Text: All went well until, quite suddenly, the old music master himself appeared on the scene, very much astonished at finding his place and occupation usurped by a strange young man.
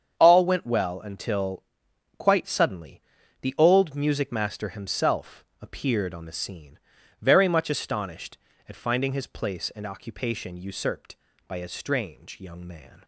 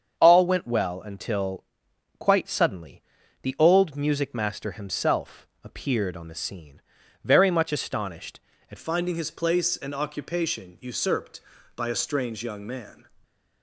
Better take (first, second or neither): first